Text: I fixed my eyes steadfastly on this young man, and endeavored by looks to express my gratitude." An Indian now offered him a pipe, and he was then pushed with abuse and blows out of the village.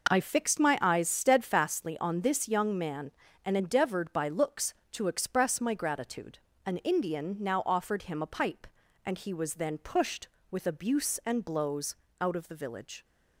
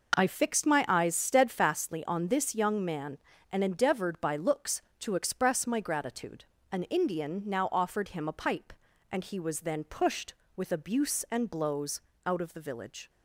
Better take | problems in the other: neither | pauses between "blows" and "out"; slight; the same in both

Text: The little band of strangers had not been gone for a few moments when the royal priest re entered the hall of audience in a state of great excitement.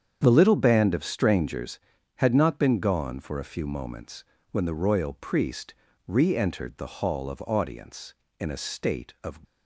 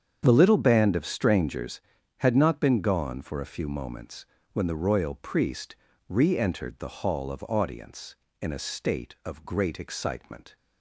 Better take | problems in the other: second | starts louder than the rest; strong; until 1.2 s; 8 dB; strong in the second // pauses between "moments" and "when"; slight; at 4.2 s; 0.30 s long; slight in the second // pauses between "priest" and "re"; slight; at 5.7 s; 0.32 s long; slight in the second // stops before "great excitement"; at 9.4 s

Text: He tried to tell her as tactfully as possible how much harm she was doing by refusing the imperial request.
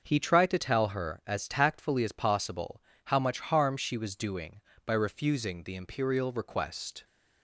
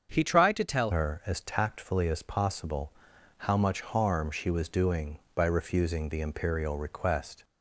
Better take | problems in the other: first | starts louder than the rest; until 1.1 s; 7 dB; also in the first // changes voice at "her"; from 0.9 s on; 6.5 s long // pauses between "possible" and "how"; noticeable; at 2.9 s; 0.46 s long; slight in the first

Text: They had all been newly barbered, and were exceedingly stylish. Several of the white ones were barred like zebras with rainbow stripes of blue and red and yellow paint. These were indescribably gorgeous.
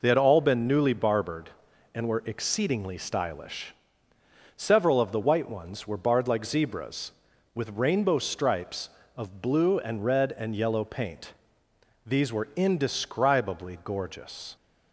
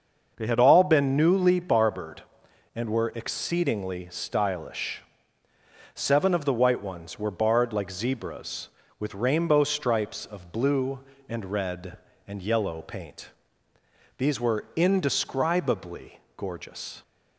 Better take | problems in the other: first | starts louder than the rest; until 1.3 s; 6.5 dB // says "Seven" for "Several"; at 5.9 s // pauses between "indescribably" and "gorgeous"; slight; at 16.1 s; 0.16 s long

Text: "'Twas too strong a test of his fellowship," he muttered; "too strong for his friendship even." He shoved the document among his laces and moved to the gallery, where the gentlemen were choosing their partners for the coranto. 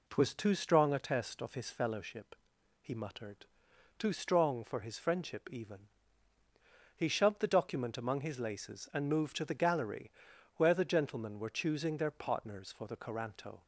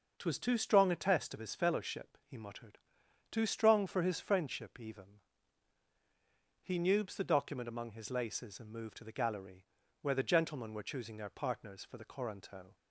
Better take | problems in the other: first | starts louder than the rest; noticeable; until 1.1 s; 6 dB // says "nubes" for "shoved"; at 6.7 s

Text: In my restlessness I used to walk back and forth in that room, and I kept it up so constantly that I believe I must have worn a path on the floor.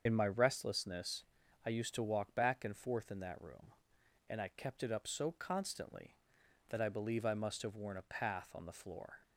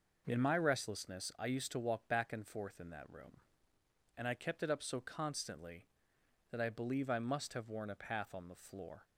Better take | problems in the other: second | loses the start of "In"; at 0.0 s; 55 ms // starts louder than the rest; until 1.0 s; 6.5 dB // pauses between "restlessness" and "I"; at 1.2 s; 0.42 s long

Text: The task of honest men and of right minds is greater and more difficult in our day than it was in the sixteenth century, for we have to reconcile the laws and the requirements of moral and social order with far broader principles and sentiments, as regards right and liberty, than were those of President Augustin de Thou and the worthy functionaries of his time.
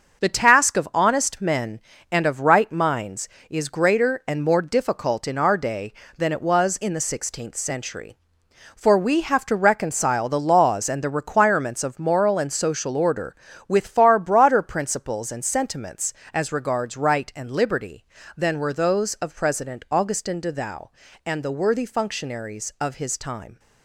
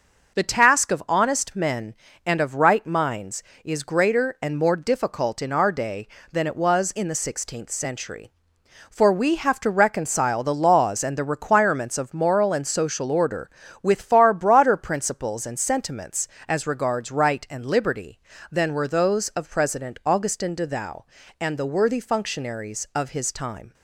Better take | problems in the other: second | gets quieter; throughout; 6.5 dB

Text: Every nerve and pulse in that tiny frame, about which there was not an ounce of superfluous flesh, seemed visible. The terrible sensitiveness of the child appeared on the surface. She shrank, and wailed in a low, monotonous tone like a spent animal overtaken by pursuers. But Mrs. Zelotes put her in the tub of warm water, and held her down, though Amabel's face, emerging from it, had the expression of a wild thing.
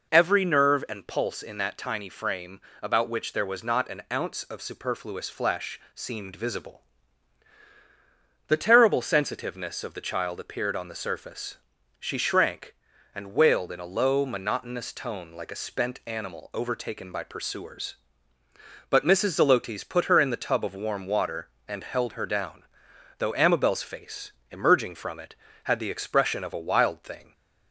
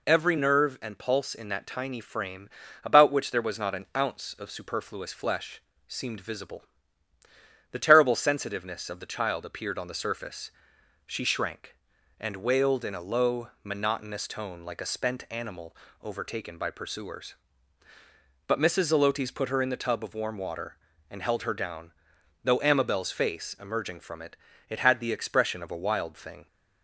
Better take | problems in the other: first | pauses between "animal" and "overtaken"; slight; at 15.7 s; 0.26 s long // says "it" twice; at 24.6 s

